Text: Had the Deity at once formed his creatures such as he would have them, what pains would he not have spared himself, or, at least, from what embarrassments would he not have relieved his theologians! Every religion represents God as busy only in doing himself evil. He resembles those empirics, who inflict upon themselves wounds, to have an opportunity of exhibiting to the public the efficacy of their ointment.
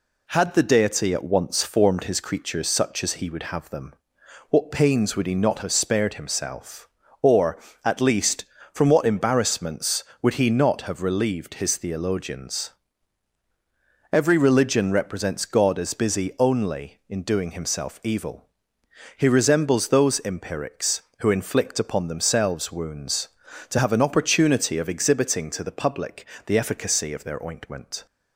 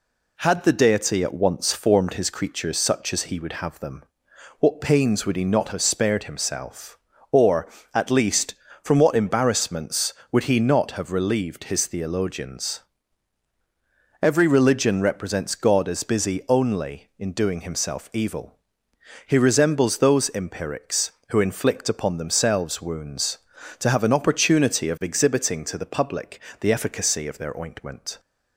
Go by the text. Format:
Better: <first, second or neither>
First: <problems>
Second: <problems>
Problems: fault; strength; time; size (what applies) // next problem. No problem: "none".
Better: neither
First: pauses between "public" and "the"; slight; at 26.2 s; 0.22 s long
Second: pauses between "public" and "the"; slight; at 26.3 s; 0.22 s long